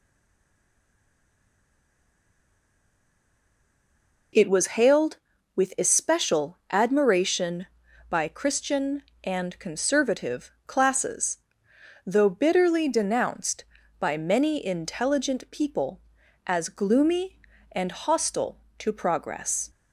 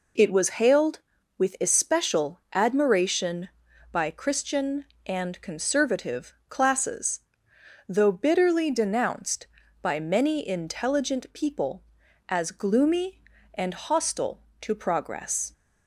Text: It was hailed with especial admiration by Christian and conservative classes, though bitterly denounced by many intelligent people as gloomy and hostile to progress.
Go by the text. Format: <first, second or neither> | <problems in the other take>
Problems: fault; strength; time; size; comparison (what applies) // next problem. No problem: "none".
second | stays silent before the first word; strong; until 4.3 s; 4.3 s long // pauses between "conservative" and "classes"; slight; at 10.4 s; 0.16 s long; slight in the second